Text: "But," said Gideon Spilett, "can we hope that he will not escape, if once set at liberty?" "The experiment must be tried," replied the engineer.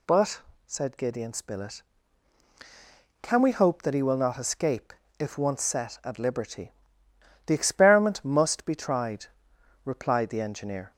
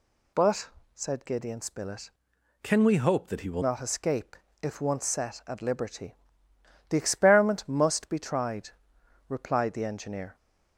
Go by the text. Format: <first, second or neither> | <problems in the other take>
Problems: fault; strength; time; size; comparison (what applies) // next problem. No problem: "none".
first | changes voice from "can" to "will"; from 2.6 to 3.6 s; 1.0 s long